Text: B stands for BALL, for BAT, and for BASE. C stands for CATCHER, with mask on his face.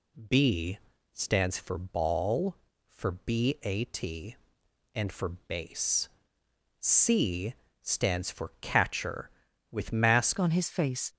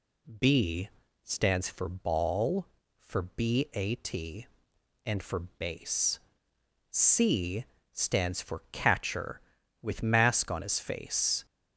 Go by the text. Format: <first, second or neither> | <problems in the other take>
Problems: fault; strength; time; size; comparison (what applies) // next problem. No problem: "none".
second | pauses between "B" and "stands"; slight; at 0.7 s; 0.34 s long; slight in the second // pauses between "C" and "stands"; slight; at 7.5 s; 0.28 s long; slight in the second // changes voice at "on"; from 10.3 s on; 0.8 s long